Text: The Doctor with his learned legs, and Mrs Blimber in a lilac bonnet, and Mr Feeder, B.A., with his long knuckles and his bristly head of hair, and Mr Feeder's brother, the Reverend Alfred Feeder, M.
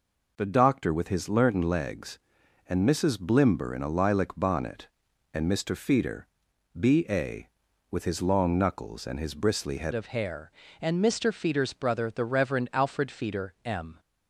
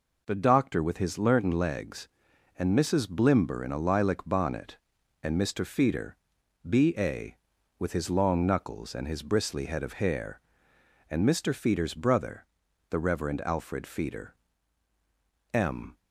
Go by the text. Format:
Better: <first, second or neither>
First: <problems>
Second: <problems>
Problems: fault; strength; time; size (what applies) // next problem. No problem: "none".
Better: second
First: changes voice at "of"; from 9.9 s on; 4.0 s long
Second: none